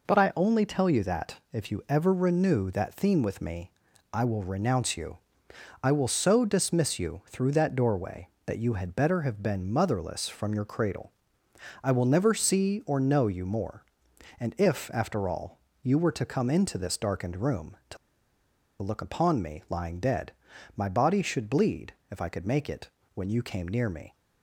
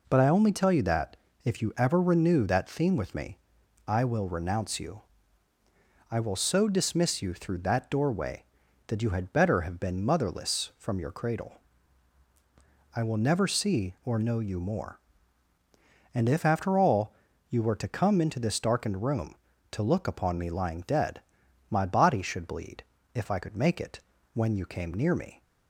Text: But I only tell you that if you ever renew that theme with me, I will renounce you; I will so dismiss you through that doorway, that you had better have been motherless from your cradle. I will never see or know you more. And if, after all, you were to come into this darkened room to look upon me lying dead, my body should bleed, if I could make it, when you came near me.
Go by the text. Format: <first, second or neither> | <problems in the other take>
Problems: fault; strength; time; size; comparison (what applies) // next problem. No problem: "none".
second | pauses between "that" and "if"; slight; at 1.3 s; 0.16 s long; slight in the second // pauses between "to" and "look"; noticeable; at 17.9 s; 0.85 s long